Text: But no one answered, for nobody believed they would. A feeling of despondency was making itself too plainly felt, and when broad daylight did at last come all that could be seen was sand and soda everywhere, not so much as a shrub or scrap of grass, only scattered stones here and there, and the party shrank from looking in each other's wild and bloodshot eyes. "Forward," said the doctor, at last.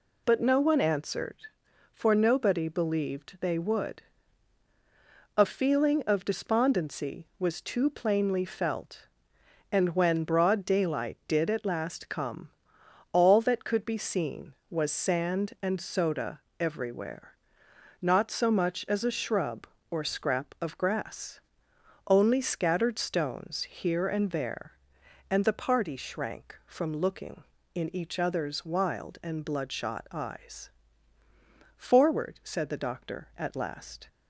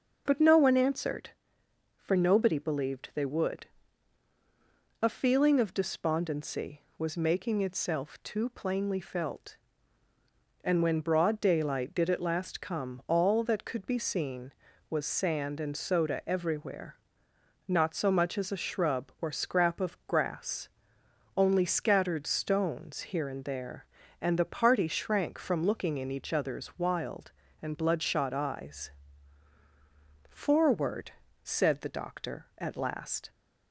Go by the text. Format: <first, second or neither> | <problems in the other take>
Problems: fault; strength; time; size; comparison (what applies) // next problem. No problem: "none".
second | skips "making itself"; at 7.5 s // pauses between "come" and "all"; noticeable; at 12.4 s; 0.62 s long // pauses between "soda" and "everywhere"; slight; at 16.3 s; 0.18 s long